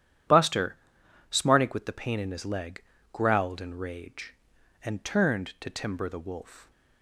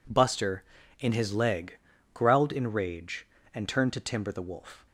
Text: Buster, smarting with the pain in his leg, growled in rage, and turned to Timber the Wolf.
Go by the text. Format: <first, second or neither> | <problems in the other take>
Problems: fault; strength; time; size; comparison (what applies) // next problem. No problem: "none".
first | skips "smarting with the pain"; at 0.8 s